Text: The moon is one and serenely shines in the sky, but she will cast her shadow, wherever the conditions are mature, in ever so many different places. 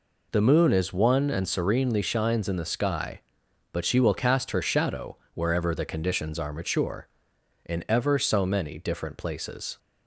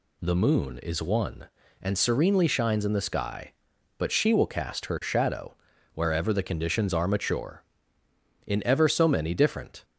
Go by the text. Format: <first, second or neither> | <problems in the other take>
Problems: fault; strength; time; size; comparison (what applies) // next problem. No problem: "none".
first | stops before "places"; at 9.8 s